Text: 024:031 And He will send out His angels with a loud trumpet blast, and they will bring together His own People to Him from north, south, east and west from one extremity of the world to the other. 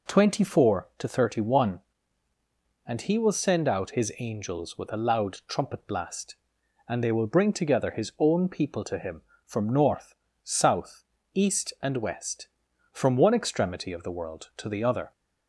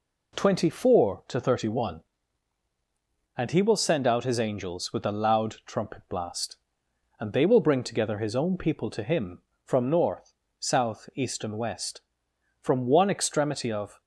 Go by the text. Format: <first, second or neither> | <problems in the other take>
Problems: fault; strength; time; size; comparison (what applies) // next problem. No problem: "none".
first | stops before "the world to the other"; at 13.9 s